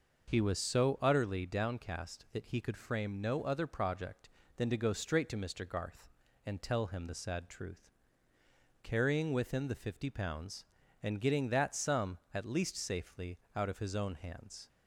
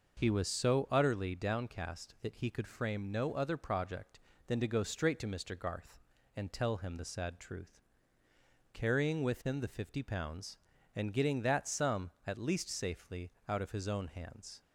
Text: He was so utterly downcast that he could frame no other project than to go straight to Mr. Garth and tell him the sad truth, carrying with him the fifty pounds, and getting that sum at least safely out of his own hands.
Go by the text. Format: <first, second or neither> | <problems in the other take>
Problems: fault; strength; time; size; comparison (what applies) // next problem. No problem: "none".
neither | pauses between "safely" and "out"; slight; the same in both